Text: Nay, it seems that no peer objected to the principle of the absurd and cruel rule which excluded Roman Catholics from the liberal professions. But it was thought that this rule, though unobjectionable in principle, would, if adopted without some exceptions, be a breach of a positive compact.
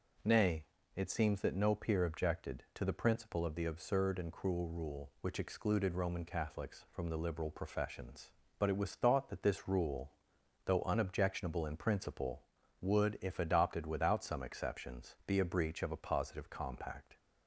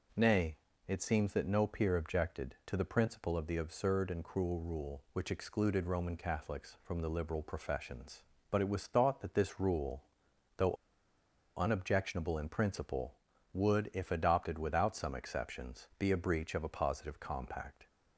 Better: first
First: none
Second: pauses between "though" and "unobjectionable"; noticeable; at 10.7 s; 0.82 s long

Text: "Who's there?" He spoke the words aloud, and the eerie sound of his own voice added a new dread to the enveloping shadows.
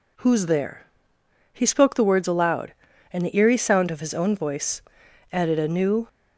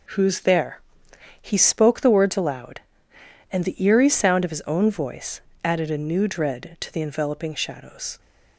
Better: second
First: pauses between "voice" and "added"; noticeable; at 4.7 s; 0.52 s long // stops before "dread to the enveloping shadows"; at 6.0 s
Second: pauses between "voice" and "added"; slight; at 5.4 s; 0.24 s long

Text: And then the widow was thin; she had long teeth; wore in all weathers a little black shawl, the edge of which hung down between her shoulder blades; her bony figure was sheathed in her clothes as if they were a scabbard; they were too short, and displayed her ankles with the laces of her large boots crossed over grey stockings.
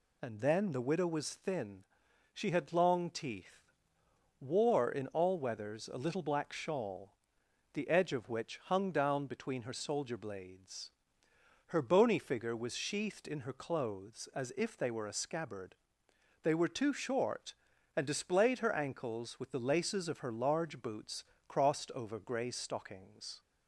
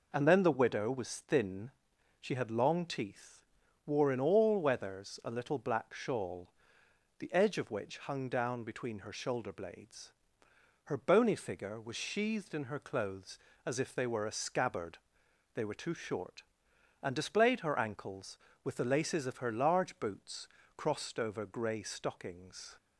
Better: second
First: says "soldier" for "shoulder"; at 9.7 s // pauses between "boots" and "crossed"; slight; at 21.2 s; 0.24 s long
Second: pauses between "boots" and "crossed"; slight; at 20.4 s; 0.30 s long

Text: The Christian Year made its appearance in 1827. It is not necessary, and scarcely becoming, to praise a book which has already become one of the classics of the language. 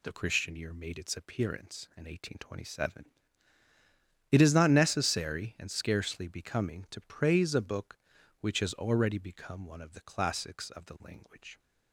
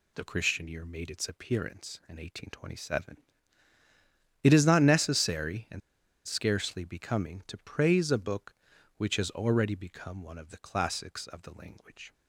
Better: first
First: none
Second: pauses between "and" and "scarcely"; noticeable; at 5.8 s; 0.46 s long

